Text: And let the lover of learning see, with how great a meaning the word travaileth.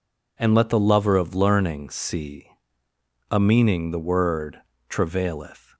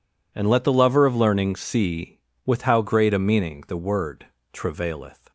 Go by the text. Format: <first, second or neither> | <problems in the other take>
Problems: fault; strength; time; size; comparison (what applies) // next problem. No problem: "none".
second | skips "with how great"; at 2.8 s // pauses between "word" and "travaileth"; slight; at 4.6 s; 0.28 s long; slight in the second